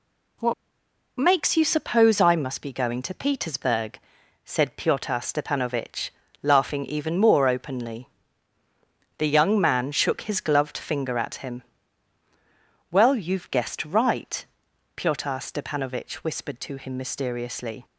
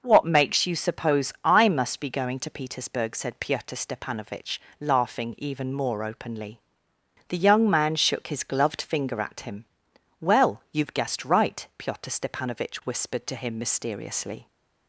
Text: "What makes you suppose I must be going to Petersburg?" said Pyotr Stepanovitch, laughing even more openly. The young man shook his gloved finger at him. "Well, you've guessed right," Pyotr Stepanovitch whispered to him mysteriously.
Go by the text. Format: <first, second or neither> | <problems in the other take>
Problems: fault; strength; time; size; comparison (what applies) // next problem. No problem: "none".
second | pauses between "What" and "makes"; noticeable; at 0.5 s; 0.65 s long